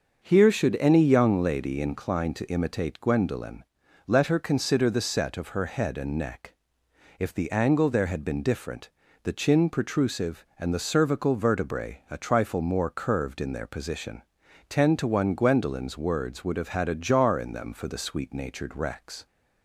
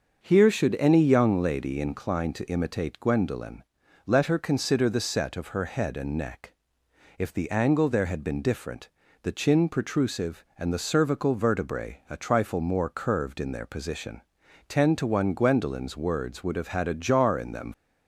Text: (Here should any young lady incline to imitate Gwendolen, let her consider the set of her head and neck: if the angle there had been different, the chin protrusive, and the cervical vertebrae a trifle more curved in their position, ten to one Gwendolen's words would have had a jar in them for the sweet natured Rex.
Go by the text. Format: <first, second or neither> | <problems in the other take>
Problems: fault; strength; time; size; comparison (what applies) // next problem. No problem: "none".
first | starts louder than the rest; until 1.2 s; 6.5 dB; also in the first // stops before "for the sweet natured Rex"; at 17.7 s